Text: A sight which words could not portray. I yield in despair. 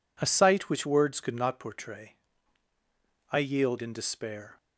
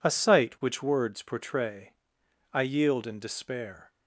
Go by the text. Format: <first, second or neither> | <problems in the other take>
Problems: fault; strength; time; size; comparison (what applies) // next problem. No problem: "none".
first | skips "could not"; at 1.2 s